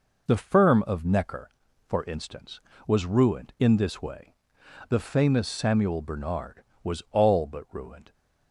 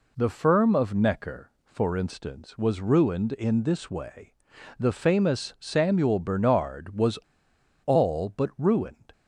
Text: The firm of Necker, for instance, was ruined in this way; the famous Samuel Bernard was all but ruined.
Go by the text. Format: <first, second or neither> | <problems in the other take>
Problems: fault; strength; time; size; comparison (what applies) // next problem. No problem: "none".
first | pauses between "was" and "all"; noticeable; at 7.1 s; 0.65 s long